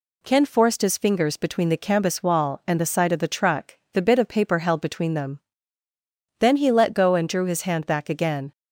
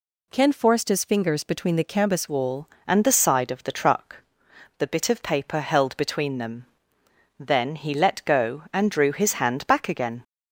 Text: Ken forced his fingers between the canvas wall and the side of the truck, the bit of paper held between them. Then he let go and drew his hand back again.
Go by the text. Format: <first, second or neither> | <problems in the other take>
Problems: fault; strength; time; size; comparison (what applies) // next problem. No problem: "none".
first | changes voice at "wall"; from 2.2 s on; 8.0 s long